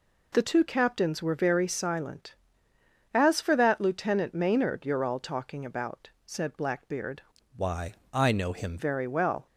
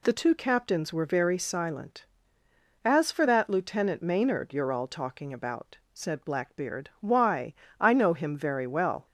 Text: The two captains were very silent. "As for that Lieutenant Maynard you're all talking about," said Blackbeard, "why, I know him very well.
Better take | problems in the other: second | changes voice from "why" to "him"; from 7.5 to 8.7 s; 1.2 s long

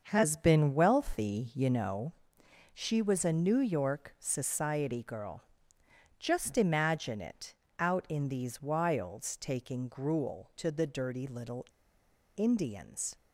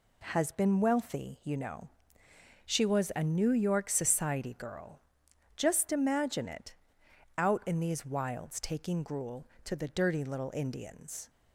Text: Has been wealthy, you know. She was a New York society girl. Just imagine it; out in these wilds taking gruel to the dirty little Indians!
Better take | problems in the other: second | starts louder than the rest; until 1.0 s; 6.5 dB // pauses between "little" and "Indians"; noticeable; at 11.6 s; 0.73 s long

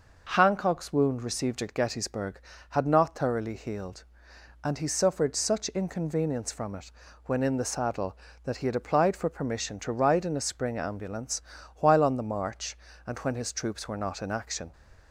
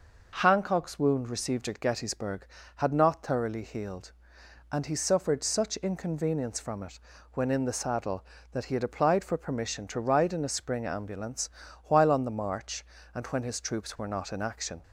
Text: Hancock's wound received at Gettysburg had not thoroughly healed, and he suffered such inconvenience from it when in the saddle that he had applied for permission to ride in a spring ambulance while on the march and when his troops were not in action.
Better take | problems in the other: neither | pauses between "it" and "when"; slight; the same in both // pauses between "ambulance" and "while"; slight; the same in both

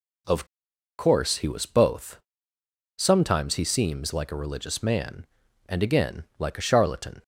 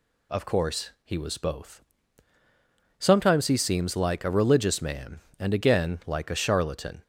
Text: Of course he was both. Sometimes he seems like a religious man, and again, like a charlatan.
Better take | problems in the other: second | pauses between "Of" and "course"; noticeable; at 0.4 s; 0.54 s long

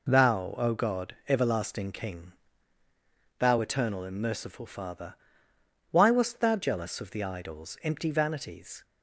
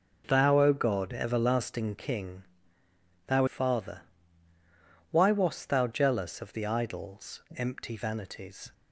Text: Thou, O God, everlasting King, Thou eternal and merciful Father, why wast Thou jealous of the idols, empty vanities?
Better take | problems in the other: first | skips "eternal and merciful"; at 3.4 s

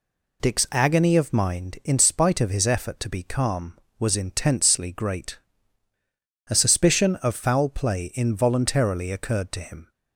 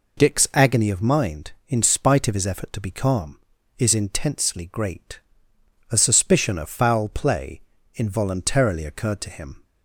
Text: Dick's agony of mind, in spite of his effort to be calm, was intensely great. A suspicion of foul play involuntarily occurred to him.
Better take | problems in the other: first | says "is" for "was"; at 3.7 s // pauses between "play" and "involuntarily"; slight; at 7.6 s; 0.34 s long

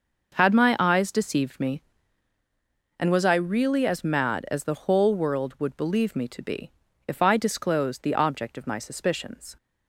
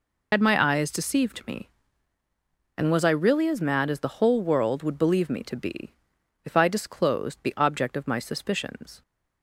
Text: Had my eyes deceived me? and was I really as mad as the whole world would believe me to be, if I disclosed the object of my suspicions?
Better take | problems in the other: first | loses the start of "Had"; at 0.3 s; 80 ms

